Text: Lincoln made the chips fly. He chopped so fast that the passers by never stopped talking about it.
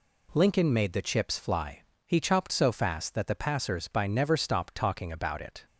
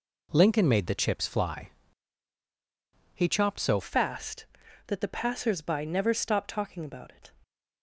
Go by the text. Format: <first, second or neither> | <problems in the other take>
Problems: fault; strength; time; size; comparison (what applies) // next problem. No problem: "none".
first | changes voice at "fast"; from 3.8 s on; 3.5 s long